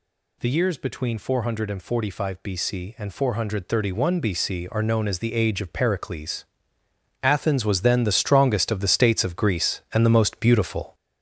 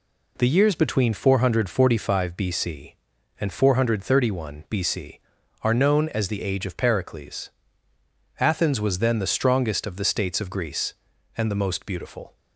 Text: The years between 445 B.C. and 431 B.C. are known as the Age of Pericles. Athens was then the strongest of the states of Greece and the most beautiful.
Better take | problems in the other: second | gets louder; noticeable; throughout; 5.5 dB

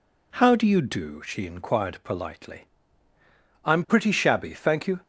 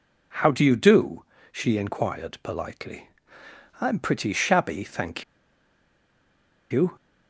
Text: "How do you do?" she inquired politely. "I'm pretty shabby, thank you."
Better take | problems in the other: first | pauses between "thank" and "you"; strong; at 5.2 s; 1.4 s long

